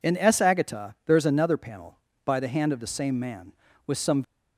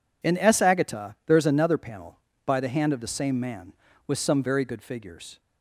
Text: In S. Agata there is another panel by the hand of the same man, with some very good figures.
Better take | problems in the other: second | stops before "very good figures"; at 4.2 s

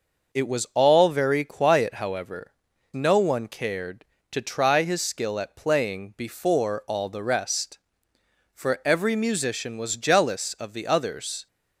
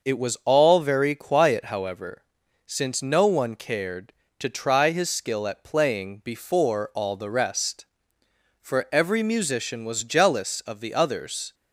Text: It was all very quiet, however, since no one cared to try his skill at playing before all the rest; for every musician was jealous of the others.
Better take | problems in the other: second | skips "since"; at 2.7 s

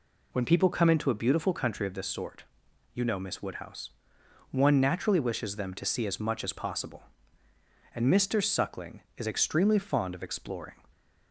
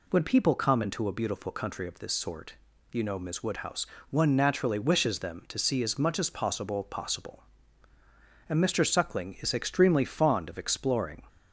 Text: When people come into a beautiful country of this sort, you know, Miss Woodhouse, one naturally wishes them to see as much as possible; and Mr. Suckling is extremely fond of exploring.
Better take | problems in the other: first | says "possible" twice; at 6.8 s

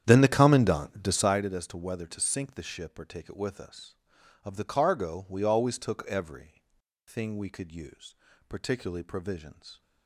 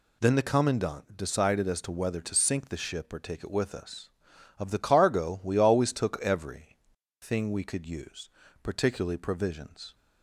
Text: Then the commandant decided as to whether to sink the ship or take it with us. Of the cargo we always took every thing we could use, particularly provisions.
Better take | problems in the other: second | starts louder than the rest; strong; until 1.5 s; 9.5 dB // pauses between "every" and "thing"; at 6.6 s; 0.44 s long; also in the second

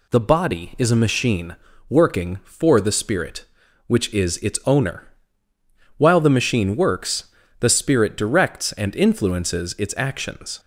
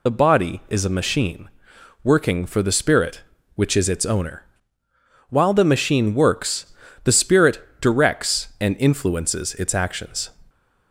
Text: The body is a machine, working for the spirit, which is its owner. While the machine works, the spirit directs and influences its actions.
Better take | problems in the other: first | loses the start of "The"; at 0.0 s; 45 ms // pauses between "spirit" and "directs"; slight; at 7.5 s; 0.22 s long

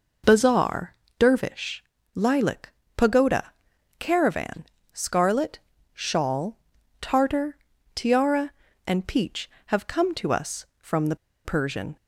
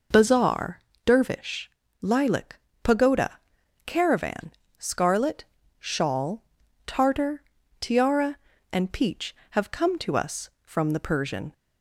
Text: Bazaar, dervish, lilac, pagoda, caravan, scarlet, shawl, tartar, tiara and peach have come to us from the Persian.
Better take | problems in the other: second | pauses between "the" and "Persian"; slight; at 11.1 s; 0.30 s long

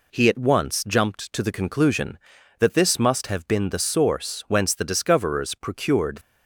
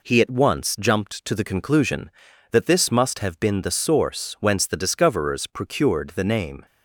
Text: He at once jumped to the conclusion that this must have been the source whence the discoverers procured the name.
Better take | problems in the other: second | stops before "the name"; at 6.2 s

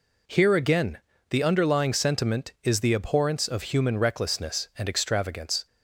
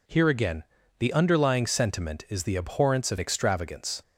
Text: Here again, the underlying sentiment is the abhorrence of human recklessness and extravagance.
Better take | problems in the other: first | skips "human recklessness and"; at 3.1 s

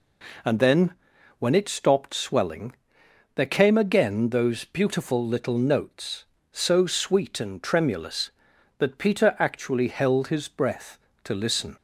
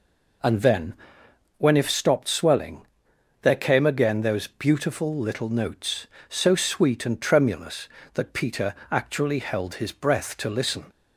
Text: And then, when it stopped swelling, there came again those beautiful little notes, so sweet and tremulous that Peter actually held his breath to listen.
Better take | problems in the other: first | says "if" for "it"; at 1.7 s // pauses between "Peter" and "actually"; slight; at 8.7 s; 0.16 s long

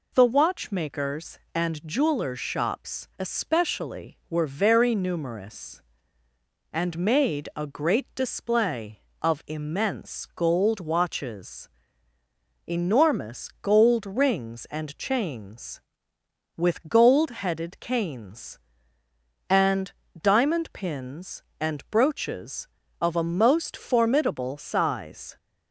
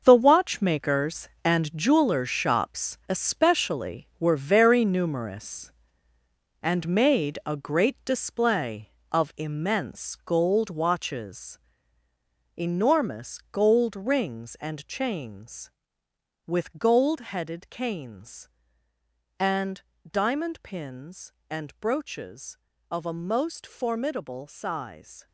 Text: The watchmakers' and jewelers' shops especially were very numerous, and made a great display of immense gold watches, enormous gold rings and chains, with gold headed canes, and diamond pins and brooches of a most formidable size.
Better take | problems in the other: first | gets quieter; strong; throughout; 11 dB // pauses between "and" and "diamond"; slight; at 19.8 s; 0.28 s long; slight in the first

